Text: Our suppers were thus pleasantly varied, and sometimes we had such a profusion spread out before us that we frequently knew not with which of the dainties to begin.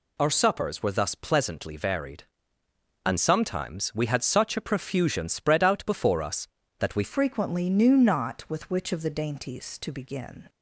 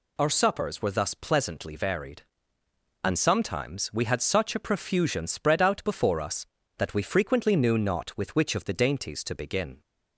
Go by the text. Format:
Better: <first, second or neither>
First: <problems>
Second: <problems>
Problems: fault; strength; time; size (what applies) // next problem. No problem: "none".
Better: second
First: changes voice at "frequently"; from 7.0 s on; 3.4 s long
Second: none